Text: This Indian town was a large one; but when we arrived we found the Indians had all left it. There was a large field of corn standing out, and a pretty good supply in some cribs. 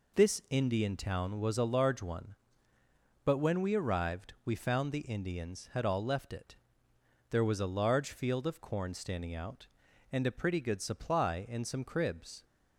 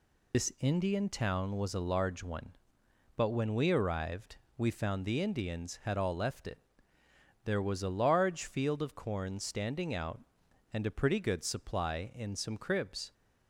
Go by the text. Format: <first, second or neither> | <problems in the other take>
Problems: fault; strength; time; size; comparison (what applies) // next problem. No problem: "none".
first | loses the start of "This"; at 0.3 s; 80 ms // pauses between "arrived" and "we"; slight; at 4.3 s; 0.22 s long